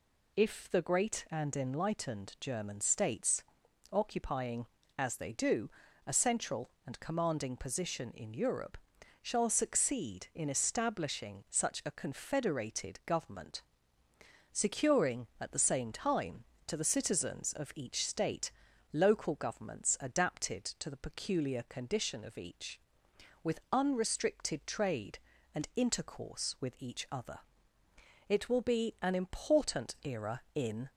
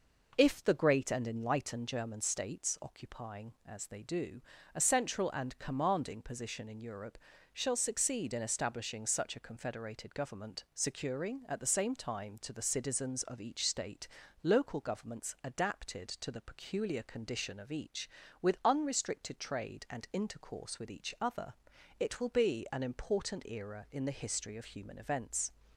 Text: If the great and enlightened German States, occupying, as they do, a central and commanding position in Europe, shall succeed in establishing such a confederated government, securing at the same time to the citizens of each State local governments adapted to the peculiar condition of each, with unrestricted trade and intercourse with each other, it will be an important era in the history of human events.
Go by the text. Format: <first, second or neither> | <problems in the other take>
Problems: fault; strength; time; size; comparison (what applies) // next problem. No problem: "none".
second | pauses between "State" and "local"; at 18.5 s; 0.40 s long; slight in the second // stops before "the history of human events"; at 30.9 s